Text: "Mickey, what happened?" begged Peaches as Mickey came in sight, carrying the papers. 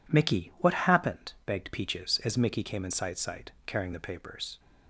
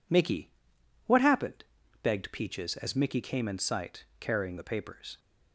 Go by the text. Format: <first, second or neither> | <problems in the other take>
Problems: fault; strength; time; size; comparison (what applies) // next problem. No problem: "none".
second | says "sight" twice; at 3.1 s